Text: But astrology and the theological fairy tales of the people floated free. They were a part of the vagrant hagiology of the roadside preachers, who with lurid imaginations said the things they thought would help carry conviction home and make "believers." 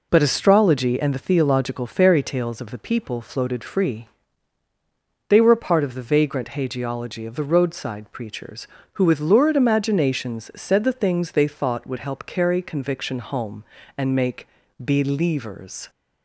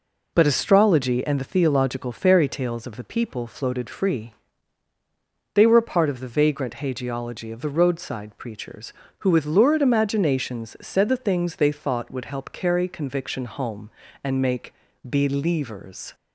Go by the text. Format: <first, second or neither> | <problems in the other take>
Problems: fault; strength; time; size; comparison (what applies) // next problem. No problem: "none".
neither | pauses between "make" and "believers"; slight; the same in both